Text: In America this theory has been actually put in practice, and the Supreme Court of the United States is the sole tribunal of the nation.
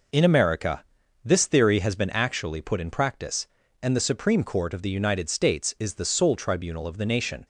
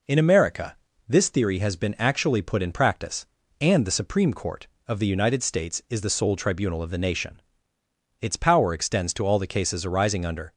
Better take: first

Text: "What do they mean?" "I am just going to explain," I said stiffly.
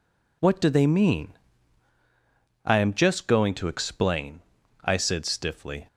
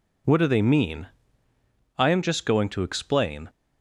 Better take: first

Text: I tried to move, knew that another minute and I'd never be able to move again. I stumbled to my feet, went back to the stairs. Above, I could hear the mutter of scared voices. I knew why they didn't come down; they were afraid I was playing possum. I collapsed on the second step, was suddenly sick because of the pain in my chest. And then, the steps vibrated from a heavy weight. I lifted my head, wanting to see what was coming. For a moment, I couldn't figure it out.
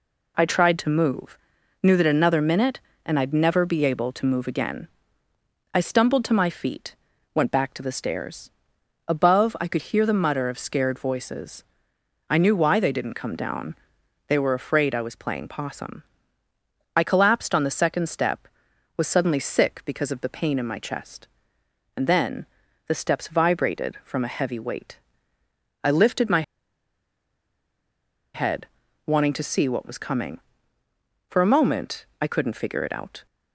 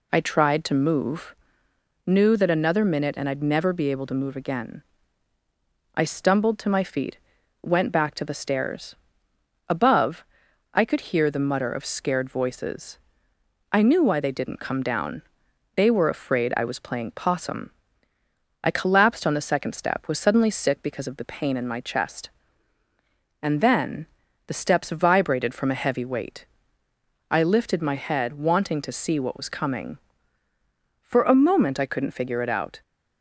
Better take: second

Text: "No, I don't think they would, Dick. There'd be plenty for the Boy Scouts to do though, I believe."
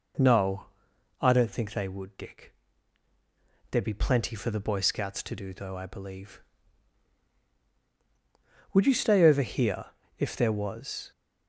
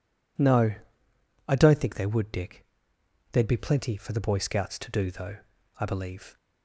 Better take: second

